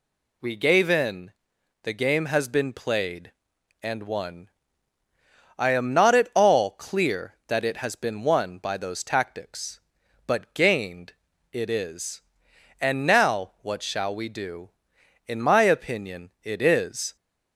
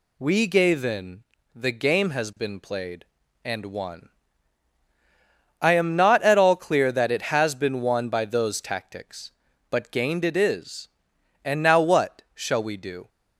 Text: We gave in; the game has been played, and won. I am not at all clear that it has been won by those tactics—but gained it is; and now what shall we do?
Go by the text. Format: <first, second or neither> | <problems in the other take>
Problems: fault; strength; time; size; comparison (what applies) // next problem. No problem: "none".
second | pauses between "gained" and "it"; at 11.1 s; 0.40 s long // goes on to say "In my opinion it is"; strong; from 15.2 s on; 1.8 s long